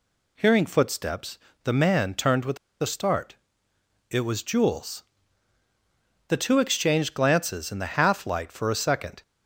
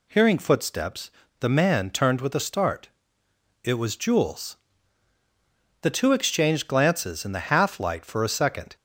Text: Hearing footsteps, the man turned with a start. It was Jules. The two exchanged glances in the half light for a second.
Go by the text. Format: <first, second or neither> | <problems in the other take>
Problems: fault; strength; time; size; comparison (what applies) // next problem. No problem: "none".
second | pauses between "with" and "a"; slight; at 2.5 s; 0.24 s long